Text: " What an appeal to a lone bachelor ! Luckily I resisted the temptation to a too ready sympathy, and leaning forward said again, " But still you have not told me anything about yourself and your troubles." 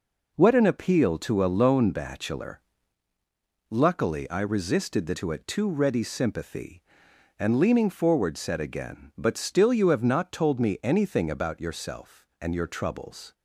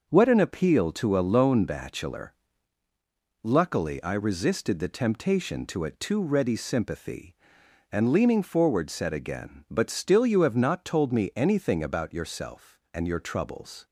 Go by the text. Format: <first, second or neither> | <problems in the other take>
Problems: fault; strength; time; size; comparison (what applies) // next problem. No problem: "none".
second | skips "temptation"; at 5.1 s